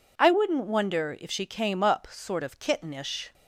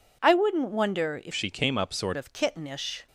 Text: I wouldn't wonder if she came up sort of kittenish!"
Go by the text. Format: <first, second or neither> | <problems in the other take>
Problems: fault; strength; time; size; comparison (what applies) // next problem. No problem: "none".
first | changes voice from "she" to "sort"; from 1.3 to 2.1 s; 0.8 s long